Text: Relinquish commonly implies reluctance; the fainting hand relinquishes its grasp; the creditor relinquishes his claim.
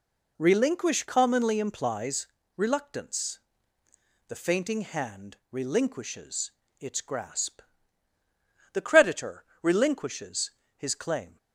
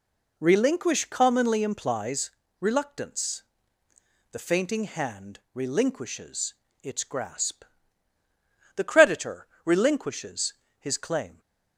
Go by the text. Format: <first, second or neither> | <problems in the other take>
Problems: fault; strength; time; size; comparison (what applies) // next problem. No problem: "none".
neither | pauses between "implies" and "reluctance"; slight; the same in both // pauses between "relinquishes" and "its"; slight; the same in both // pauses between "creditor" and "relinquishes"; slight; the same in both // pauses between "relinquishes" and "his"; slight; the same in both